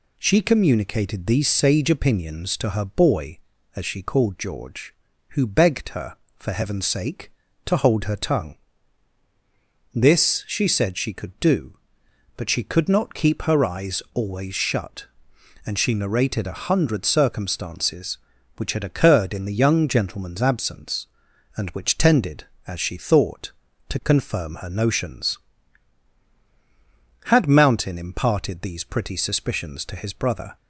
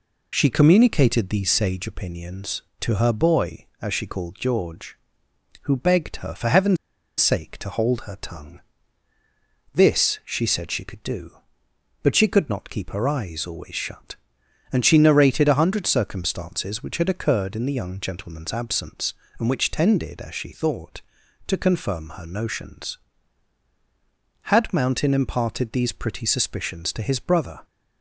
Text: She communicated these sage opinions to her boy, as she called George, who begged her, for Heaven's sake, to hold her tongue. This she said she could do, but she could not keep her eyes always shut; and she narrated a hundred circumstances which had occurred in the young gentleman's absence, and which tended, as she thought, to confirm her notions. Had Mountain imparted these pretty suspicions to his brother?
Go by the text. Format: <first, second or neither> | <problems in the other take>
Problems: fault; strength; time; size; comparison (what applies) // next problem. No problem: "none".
first | pauses between "Heaven's" and "sake"; at 6.7 s; 0.43 s long